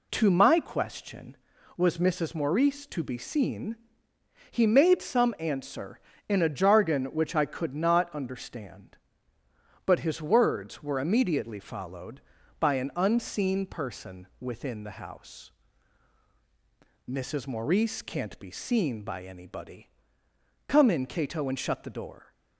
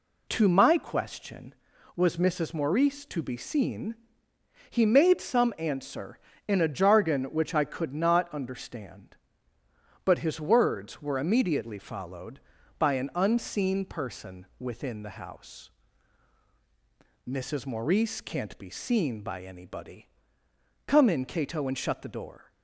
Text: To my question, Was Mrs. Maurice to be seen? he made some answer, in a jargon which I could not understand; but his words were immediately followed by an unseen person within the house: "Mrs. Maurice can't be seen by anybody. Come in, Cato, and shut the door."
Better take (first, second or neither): neither